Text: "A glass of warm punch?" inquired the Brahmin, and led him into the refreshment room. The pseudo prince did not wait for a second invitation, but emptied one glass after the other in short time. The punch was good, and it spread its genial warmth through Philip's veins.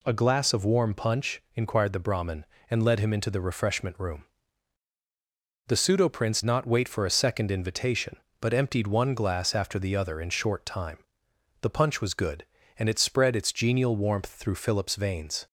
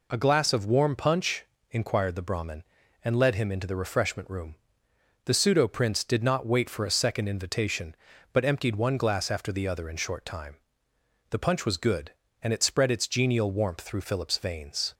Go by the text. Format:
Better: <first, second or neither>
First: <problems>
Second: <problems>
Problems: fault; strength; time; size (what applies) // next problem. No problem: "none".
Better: second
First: skips "did"; at 6.4 s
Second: none